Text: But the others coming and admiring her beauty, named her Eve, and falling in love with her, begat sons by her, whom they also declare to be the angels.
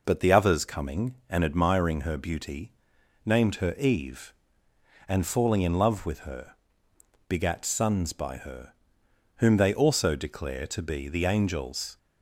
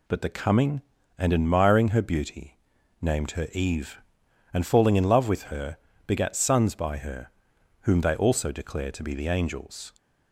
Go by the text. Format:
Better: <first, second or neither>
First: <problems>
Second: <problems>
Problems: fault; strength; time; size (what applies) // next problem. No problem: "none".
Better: first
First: none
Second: skips "others"; at 0.3 s